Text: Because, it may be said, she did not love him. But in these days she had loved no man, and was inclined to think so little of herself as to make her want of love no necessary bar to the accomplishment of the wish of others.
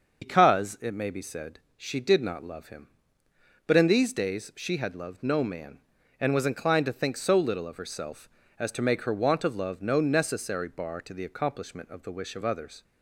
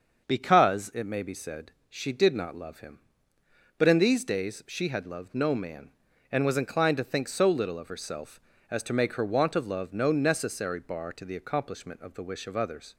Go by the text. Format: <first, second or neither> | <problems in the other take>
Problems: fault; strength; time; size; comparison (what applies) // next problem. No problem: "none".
second | loses the start of "Because"; at 0.2 s; 100 ms // starts louder than the rest; until 1.2 s; 6.5 dB; also in the second